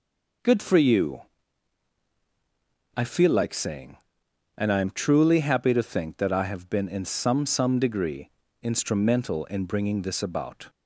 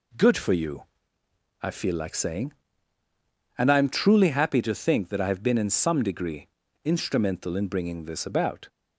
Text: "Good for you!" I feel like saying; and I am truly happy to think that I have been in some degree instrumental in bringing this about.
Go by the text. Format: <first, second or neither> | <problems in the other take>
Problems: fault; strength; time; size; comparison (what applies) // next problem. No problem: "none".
second | says "some" twice; at 7.4 s // pauses between "degree" and "instrumental"; slight; at 8.2 s; 0.32 s long; slight in the second